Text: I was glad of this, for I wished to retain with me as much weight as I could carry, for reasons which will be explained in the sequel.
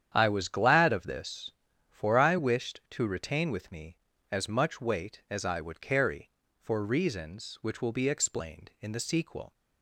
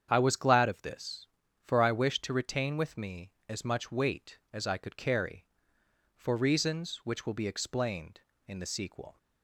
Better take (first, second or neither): second